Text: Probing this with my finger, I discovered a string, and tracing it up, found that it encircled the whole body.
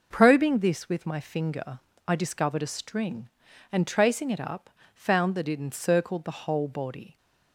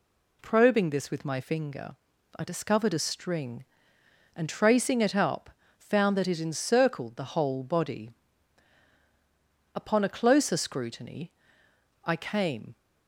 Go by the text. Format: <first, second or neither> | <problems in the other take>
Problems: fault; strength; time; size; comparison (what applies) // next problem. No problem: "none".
first | goes on to say "Upon a closer scrutiny I came"; strong; from 9.7 s on; 3.0 s long